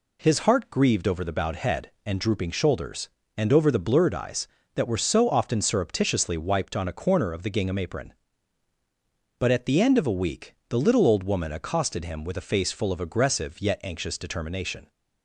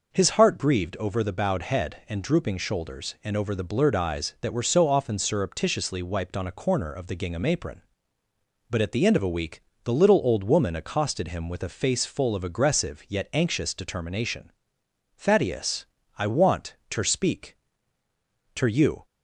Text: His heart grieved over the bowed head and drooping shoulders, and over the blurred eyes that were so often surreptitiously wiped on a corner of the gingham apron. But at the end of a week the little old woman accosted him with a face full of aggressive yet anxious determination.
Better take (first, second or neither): first